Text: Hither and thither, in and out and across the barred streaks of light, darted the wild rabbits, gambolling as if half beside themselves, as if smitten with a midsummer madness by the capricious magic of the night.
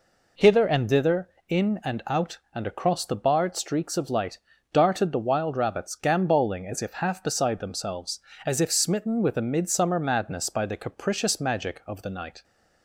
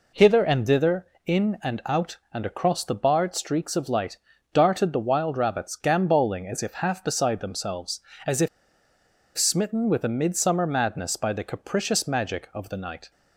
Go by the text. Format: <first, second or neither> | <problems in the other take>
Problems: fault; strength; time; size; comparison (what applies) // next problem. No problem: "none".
first | pauses between "if" and "smitten"; noticeable; at 8.4 s; 0.89 s long